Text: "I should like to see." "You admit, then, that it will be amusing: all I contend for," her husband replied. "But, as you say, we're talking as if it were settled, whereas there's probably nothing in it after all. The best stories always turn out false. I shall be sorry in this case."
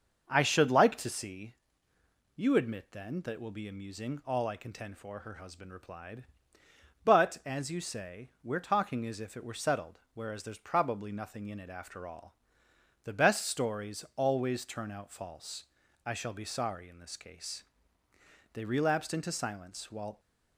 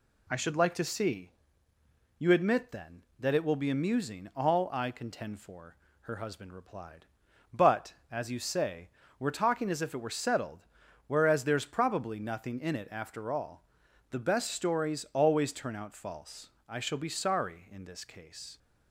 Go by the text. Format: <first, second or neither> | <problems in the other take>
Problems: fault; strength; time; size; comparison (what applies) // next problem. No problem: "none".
second | starts louder than the rest; until 1.2 s; 6.5 dB // goes on to say "They relapsed into silence while"; from 18.5 s on; 1.6 s long